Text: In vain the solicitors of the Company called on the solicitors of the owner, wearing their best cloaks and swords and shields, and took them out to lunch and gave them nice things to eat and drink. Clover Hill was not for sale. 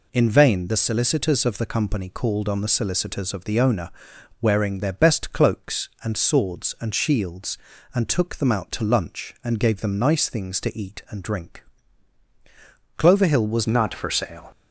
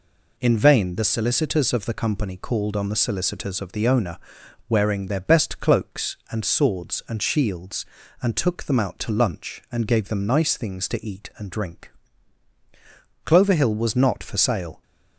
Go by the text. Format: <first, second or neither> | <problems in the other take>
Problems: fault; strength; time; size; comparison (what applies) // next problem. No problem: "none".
second | changes voice at "not"; from 13.6 s on; 0.8 s long